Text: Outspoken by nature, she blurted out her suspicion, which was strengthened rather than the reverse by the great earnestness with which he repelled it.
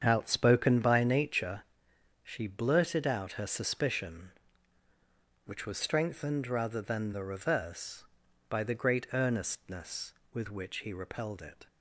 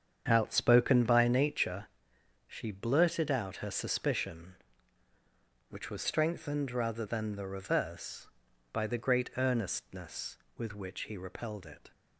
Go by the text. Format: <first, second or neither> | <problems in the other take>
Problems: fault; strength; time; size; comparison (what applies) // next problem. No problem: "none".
neither | starts louder than the rest; strong; the same in both